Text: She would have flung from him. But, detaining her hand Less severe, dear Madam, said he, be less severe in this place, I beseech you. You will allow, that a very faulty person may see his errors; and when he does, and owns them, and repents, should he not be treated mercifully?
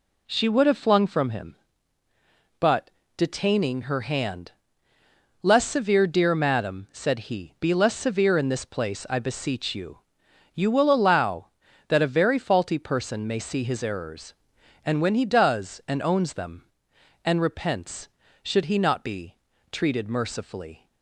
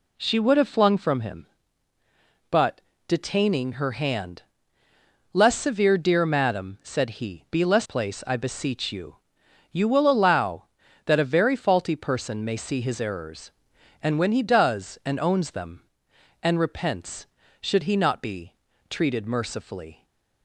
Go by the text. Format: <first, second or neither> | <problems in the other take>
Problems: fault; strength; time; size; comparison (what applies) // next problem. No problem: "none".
first | pauses between "hand" and "Less"; noticeable; at 4.4 s; 0.92 s long; noticeable in the first // skips "severe in this"; at 7.8 s // pauses between "be" and "treated"; slight; at 18.5 s; 0.36 s long; slight in the first